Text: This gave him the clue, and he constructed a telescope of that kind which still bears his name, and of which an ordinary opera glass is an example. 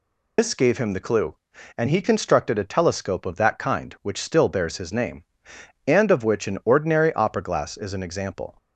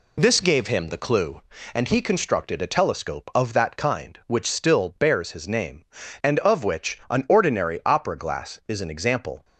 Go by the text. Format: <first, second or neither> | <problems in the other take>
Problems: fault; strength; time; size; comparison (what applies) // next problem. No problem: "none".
second | loses the start of "This"; at 0.3 s; 140 ms